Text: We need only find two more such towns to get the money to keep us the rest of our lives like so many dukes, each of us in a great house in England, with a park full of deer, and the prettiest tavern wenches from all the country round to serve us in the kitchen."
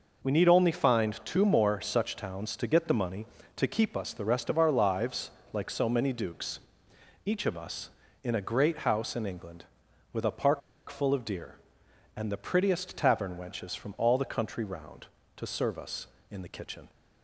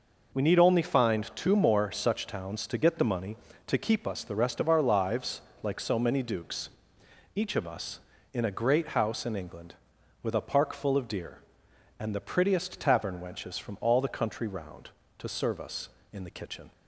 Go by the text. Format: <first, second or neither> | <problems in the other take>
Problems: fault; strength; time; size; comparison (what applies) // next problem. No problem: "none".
second | pauses between "lives" and "like"; slight; at 5.3 s; 0.20 s long; slight in the second // pauses between "park" and "full"; slight; at 10.6 s; 0.28 s long